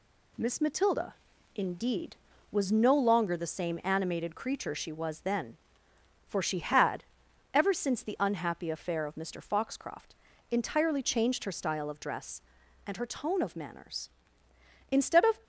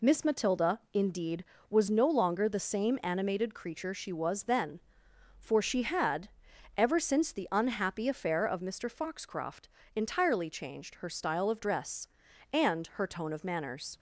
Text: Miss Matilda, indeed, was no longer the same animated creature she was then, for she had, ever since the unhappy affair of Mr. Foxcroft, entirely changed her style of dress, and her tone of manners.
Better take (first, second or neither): second